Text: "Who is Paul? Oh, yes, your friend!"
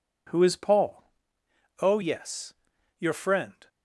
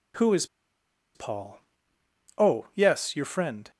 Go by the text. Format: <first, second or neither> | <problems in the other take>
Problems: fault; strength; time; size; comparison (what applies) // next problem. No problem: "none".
first | pauses between "is" and "Paul"; noticeable; at 0.4 s; 0.69 s long